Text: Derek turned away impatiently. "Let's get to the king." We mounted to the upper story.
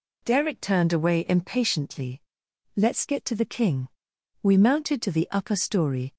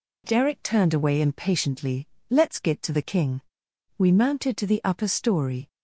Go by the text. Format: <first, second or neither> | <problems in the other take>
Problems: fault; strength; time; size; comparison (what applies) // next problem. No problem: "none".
neither | none